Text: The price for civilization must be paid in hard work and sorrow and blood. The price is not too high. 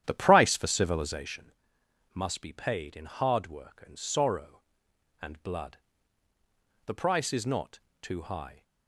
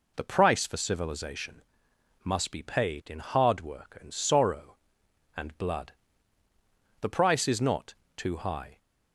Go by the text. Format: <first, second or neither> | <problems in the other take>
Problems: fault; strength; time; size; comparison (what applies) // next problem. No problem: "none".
second | starts louder than the rest; strong; until 1.4 s; 10.5 dB // pauses between "civilization" and "must"; noticeable; at 1.5 s; 0.62 s long; noticeable in the second // pauses between "not" and "too"; slight; at 7.7 s; 0.22 s long; slight in the second